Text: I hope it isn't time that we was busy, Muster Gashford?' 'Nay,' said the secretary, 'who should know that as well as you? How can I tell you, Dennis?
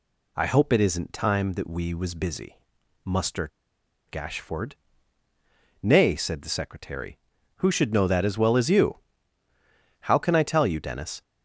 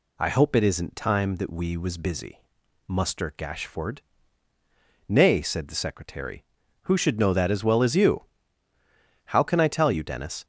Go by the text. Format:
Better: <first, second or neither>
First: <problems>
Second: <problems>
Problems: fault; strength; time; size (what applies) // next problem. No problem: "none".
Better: second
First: pauses between "Muster" and "Gashford"; noticeable; at 3.5 s; 0.60 s long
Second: none